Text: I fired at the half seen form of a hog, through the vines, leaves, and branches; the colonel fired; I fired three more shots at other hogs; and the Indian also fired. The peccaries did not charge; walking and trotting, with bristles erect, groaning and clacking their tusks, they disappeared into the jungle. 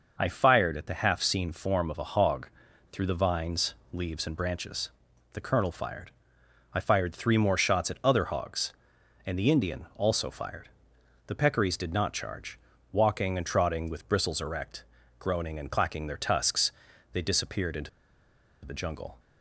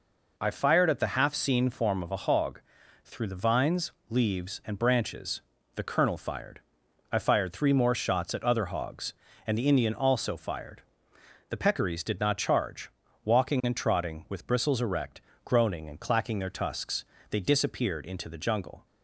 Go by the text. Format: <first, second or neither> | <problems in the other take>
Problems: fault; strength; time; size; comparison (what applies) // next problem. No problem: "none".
second | pauses between "into" and "the"; noticeable; at 17.8 s; 0.75 s long